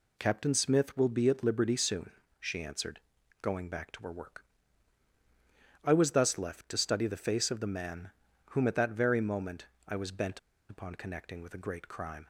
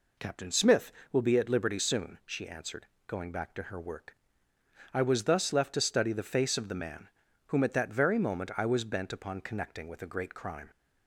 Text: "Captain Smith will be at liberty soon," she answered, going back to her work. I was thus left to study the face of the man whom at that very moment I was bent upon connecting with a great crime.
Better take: second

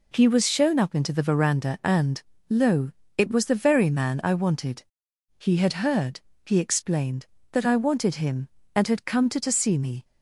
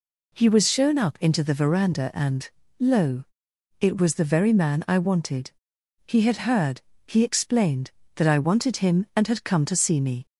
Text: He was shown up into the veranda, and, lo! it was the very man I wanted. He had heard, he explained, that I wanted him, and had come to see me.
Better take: second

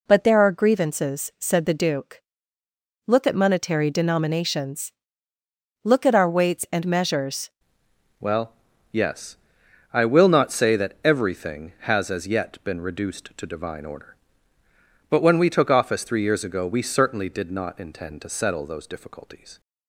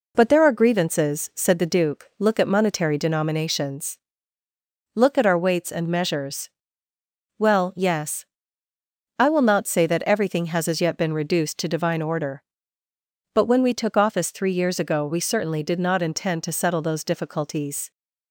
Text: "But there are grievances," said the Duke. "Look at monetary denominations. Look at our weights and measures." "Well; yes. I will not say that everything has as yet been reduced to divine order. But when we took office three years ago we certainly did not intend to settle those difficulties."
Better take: second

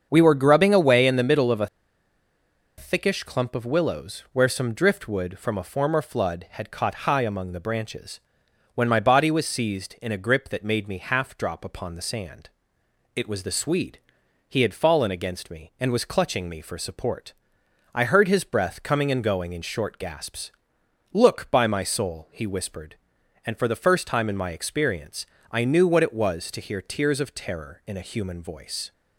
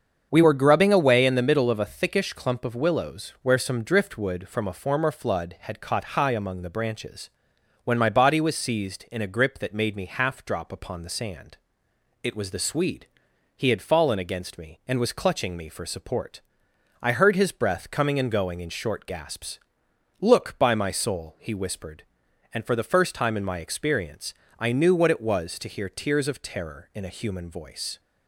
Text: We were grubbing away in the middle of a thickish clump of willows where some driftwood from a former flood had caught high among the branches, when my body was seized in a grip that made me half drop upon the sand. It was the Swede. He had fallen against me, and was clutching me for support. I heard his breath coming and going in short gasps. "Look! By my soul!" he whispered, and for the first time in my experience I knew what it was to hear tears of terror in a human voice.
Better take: second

